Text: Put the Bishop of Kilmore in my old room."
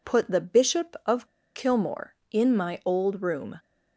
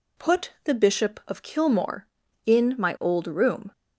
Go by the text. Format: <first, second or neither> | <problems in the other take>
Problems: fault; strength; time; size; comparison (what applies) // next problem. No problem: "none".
second | pauses between "of" and "Kilmore"; slight; at 1.2 s; 0.28 s long